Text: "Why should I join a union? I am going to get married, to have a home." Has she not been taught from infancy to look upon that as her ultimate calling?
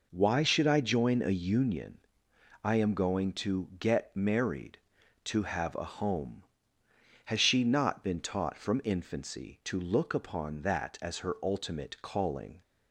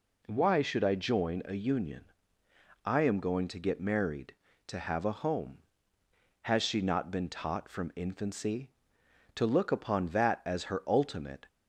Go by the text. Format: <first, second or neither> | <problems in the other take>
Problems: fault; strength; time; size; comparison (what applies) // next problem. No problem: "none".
first | stops before "calling"; at 11.4 s